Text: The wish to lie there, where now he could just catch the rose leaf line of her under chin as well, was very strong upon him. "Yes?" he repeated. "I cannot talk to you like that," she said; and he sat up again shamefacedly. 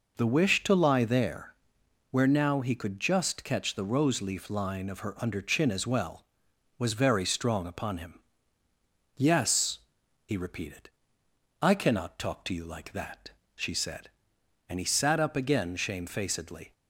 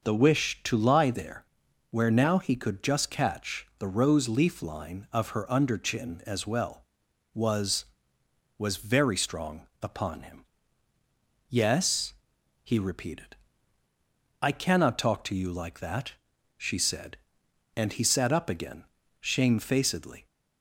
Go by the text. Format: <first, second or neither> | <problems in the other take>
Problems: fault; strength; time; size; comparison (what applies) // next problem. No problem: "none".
first | says "was" twice; at 8.5 s // pauses between "strong" and "upon"; slight; at 9.6 s; 0.16 s long // pauses between "again" and "shamefacedly"; at 18.8 s; 0.38 s long